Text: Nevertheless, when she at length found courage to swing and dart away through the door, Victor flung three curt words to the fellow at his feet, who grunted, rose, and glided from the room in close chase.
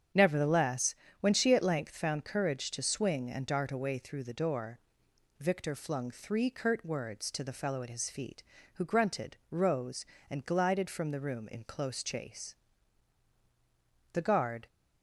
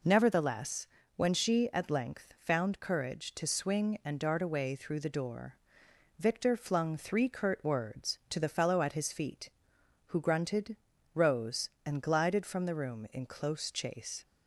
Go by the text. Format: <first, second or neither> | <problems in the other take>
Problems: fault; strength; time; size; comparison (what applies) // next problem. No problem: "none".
second | starts louder than the rest; strong; until 1.4 s; 8.5 dB // goes on to say "The guard"; from 14.1 s on; 0.54 s long